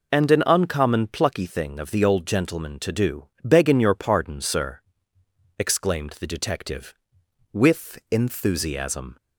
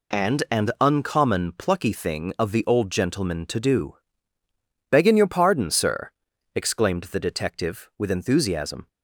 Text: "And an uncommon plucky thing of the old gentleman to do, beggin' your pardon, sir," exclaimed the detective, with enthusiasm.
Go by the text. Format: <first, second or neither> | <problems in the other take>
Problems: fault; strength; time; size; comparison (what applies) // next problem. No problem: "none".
neither | none